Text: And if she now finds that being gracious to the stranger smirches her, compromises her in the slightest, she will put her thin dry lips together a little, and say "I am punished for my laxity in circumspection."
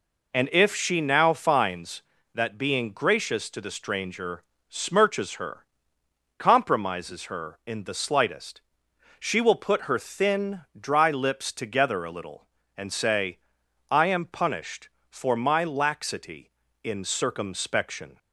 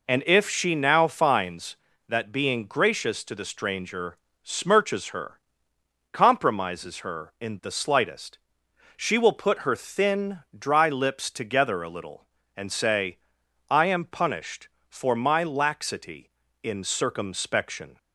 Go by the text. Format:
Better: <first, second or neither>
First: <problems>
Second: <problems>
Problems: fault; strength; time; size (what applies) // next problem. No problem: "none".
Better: neither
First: pauses between "stranger" and "smirches"; slight; at 4.4 s; 0.28 s long // pauses between "thin" and "dry"; slight; at 10.6 s; 0.18 s long // pauses between "say" and "I"; noticeable; at 13.3 s; 0.52 s long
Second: pauses between "stranger" and "smirches"; slight; at 4.1 s; 0.28 s long // pauses between "thin" and "dry"; slight; at 10.3 s; 0.18 s long // pauses between "say" and "I"; noticeable; at 13.1 s; 0.52 s long